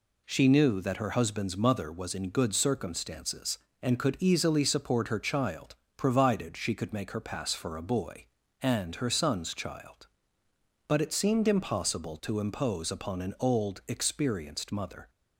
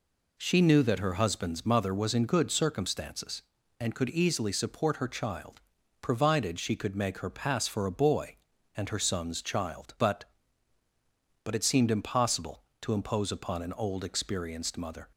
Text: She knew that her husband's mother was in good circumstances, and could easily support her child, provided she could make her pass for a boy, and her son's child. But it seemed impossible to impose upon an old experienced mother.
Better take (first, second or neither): first